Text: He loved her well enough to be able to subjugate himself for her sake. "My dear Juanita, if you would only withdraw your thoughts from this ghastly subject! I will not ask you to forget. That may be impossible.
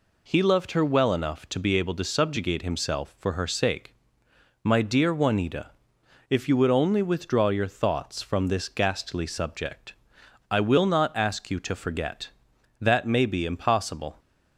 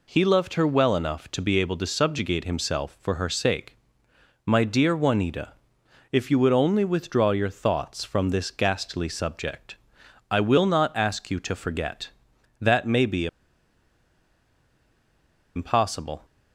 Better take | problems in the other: first | pauses between "be" and "impossible"; strong; at 13.2 s; 2.2 s long

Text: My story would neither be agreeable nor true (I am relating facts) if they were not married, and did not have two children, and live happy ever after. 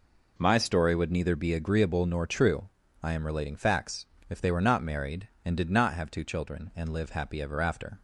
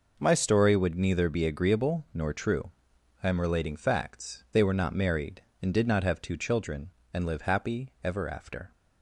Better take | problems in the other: first | skips "if"; at 4.4 s

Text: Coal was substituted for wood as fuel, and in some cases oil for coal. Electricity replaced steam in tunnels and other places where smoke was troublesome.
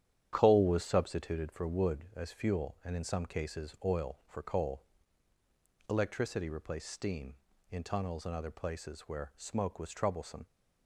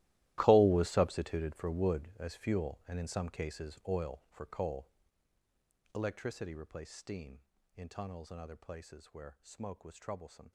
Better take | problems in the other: first | gets quieter; strong; throughout; 18.5 dB // starts louder than the rest; strong; until 1.3 s; 15.5 dB; strong in the first

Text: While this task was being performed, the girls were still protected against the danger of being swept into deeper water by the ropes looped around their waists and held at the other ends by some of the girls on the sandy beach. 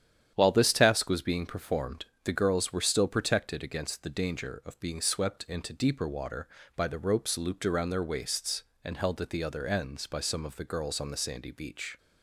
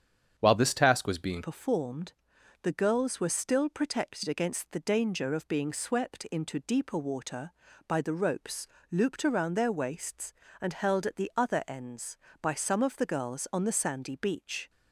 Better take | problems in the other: first | starts louder than the rest; strong; until 1.3 s; 8.5 dB; strong in the first // changes voice at "performed"; from 1.4 s on; 13.2 s long // pauses between "ropes" and "looped"; slight; at 8.6 s; 0.24 s long

